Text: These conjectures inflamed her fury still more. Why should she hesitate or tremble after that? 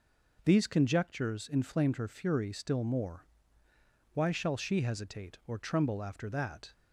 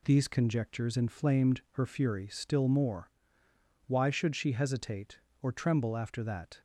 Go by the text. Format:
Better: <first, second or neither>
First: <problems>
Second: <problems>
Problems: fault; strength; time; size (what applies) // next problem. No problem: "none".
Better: second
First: says "shall" for "should"; at 4.3 s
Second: none